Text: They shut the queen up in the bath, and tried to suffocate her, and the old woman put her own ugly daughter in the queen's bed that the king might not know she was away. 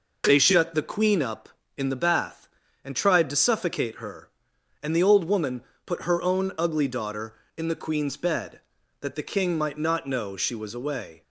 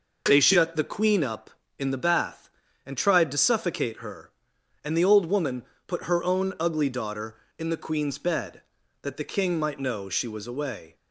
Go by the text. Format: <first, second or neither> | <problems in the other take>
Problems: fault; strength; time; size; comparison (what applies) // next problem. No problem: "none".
first | pauses between "woman" and "put"; slight; at 5.6 s; 0.24 s long; slight in the first // skips "not"; at 9.7 s